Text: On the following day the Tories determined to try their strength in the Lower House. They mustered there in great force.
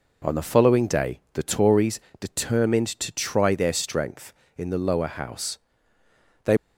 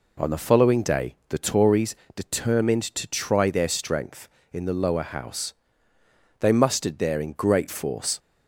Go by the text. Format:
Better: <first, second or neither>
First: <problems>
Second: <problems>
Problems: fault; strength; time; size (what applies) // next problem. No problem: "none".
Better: second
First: pauses between "Tories" and "determined"; slight; at 1.9 s; 0.22 s long // stops before "mustered there in great force"; at 6.5 s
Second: pauses between "Tories" and "determined"; slight; at 1.9 s; 0.22 s long